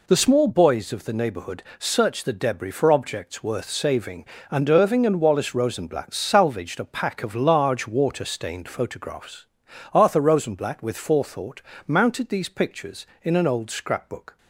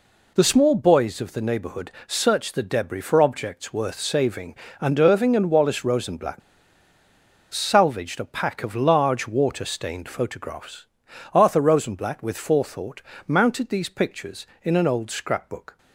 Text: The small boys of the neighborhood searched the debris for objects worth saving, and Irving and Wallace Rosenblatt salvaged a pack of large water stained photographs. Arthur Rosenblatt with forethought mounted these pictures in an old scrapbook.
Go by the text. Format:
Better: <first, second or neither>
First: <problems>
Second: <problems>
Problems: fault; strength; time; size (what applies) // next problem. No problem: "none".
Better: first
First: pauses between "neighborhood" and "searched"; slight; at 1.6 s; 0.16 s long // pauses between "forethought" and "mounted"; slight; at 11.6 s; 0.24 s long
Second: pauses between "neighborhood" and "searched"; slight; at 1.8 s; 0.16 s long // pauses between "Rosenblatt" and "salvaged"; at 6.4 s; 1.1 s long // pauses between "forethought" and "mounted"; slight; at 13.0 s; 0.24 s long